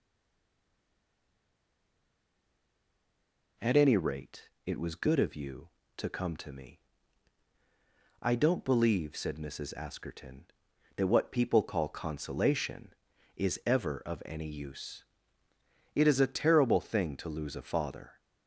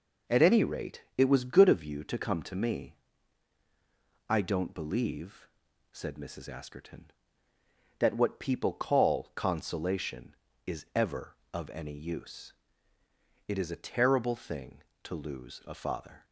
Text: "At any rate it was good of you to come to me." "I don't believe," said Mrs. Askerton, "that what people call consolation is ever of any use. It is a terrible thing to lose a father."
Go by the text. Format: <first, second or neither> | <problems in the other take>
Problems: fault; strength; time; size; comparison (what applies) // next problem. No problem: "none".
second | stays silent before the first word; strong; until 3.5 s; 3.5 s long // pauses between "rate" and "it"; slight; at 4.4 s; 0.18 s long